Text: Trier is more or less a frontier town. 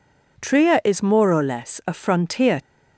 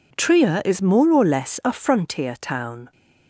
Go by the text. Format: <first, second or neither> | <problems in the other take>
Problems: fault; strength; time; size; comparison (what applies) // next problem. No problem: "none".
second | stops before "town"; at 2.6 s